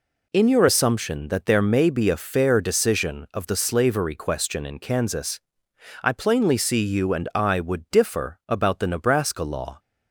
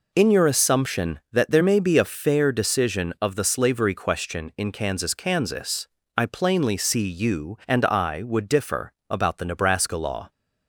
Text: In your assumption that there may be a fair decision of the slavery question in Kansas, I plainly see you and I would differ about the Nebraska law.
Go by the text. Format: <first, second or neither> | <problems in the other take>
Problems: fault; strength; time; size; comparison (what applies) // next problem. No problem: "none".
first | says "Kansas" twice; at 5.1 s // pauses between "differ" and "about"; slight; at 8.9 s; 0.16 s long